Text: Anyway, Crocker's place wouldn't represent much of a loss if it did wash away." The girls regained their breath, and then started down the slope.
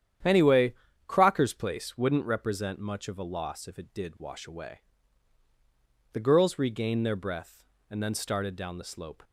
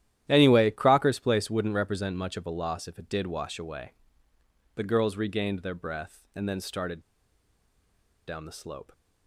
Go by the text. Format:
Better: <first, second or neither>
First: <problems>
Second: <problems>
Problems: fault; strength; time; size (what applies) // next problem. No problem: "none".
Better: first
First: starts louder than the rest; strong; until 1.5 s; 9.5 dB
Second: starts louder than the rest; strong; until 1.2 s; 12 dB // pauses between "started" and "down"; strong; at 7.0 s; 1.2 s long